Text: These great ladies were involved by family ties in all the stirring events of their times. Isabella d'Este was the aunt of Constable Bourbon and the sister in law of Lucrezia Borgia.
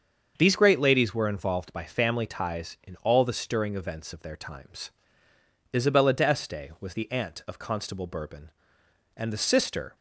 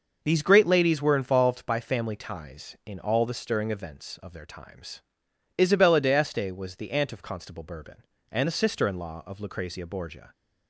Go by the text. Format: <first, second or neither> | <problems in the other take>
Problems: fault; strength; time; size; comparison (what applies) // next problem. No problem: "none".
second | starts louder than the rest; until 1.3 s; 7 dB; noticeable in the second // stops before "in law of Lucrezia Borgia"; at 9.9 s